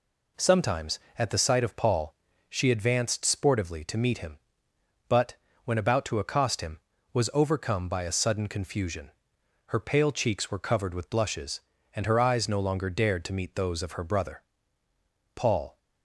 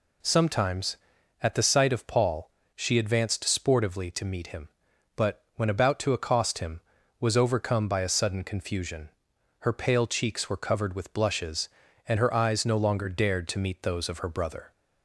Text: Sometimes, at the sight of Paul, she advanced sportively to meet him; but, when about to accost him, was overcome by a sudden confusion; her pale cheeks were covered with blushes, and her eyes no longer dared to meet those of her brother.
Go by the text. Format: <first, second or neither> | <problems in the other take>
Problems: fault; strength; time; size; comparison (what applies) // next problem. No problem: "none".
second | goes on to say "Paul"; slight; from 15.3 s on; 0.42 s long